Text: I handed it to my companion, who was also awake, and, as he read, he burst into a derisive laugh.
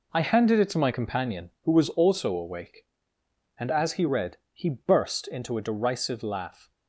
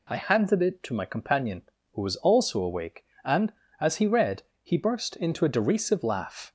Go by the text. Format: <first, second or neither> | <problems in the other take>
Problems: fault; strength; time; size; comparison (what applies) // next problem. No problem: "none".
second | gets quieter; strong; throughout; 10.5 dB